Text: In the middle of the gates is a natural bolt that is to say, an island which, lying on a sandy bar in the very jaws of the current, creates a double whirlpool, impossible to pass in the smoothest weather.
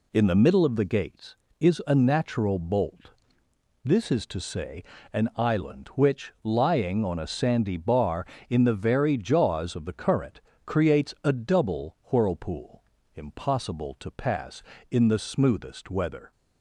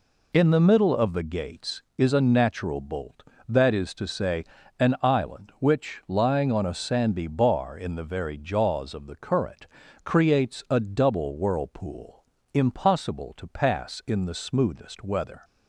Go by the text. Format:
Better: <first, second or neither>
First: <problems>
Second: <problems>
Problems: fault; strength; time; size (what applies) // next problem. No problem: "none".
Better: second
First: says "this" for "that"; at 3.8 s // pauses between "double" and "whirlpool"; slight; at 11.9 s; 0.16 s long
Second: none